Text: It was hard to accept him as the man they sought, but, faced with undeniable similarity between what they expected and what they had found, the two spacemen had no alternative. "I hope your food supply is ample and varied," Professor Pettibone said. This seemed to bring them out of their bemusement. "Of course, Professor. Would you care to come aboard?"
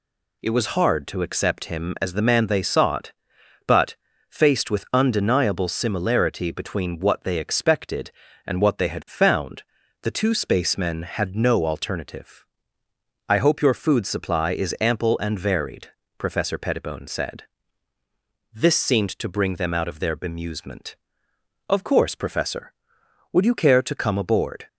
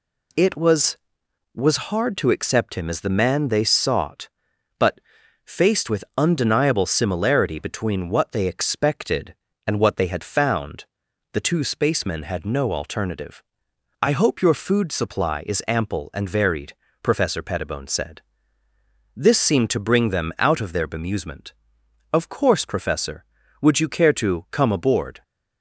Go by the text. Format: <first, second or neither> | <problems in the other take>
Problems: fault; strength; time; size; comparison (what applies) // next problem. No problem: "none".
first | says "was" twice; at 1.5 s